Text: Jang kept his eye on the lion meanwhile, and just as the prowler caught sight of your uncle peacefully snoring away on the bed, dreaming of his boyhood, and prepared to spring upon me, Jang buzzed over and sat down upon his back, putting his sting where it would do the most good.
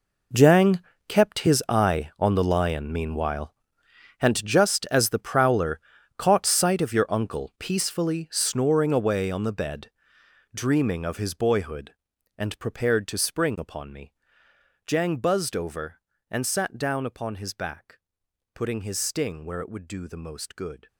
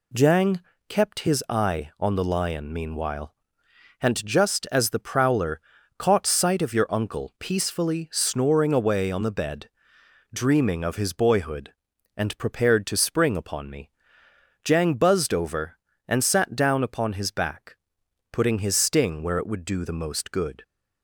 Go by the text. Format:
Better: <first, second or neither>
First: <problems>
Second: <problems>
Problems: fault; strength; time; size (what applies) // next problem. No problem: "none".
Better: second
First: gets quieter; strong; throughout; 16 dB // pauses between "Jang" and "kept"; slight; at 0.7 s; 0.28 s long // pauses between "prowler" and "caught"; at 5.7 s; 0.38 s long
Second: pauses between "Jang" and "kept"; slight; at 0.6 s; 0.28 s long // pauses between "prowler" and "caught"; at 5.6 s; 0.38 s long